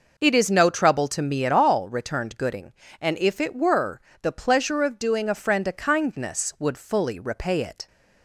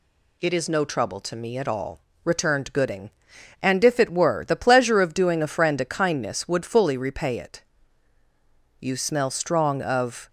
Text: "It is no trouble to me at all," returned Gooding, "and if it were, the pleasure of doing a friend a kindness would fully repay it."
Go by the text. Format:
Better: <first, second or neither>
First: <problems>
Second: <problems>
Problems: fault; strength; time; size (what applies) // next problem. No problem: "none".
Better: first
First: none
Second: goes on to say "You smell strong of"; from 8.8 s on; 1.4 s long